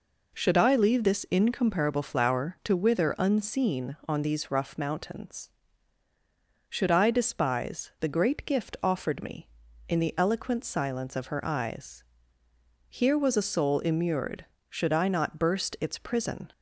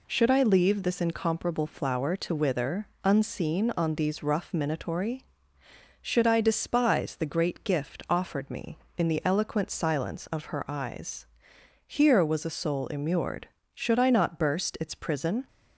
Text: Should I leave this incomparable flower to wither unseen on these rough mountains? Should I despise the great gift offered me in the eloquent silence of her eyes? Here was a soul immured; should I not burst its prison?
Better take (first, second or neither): first